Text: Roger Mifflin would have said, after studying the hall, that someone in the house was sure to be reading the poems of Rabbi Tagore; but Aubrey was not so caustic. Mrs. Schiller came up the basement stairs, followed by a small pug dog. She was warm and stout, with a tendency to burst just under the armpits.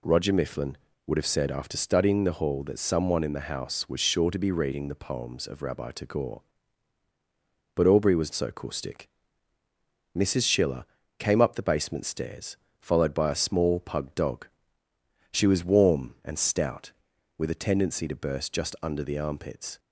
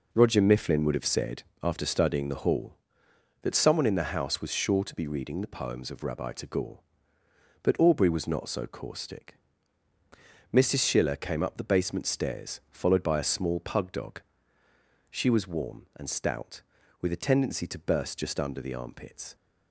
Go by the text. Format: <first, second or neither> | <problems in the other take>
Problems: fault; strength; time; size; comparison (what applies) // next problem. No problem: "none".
second | skips "not"; at 8.3 s // pauses between "Schiller" and "came"; slight; at 10.8 s; 0.34 s long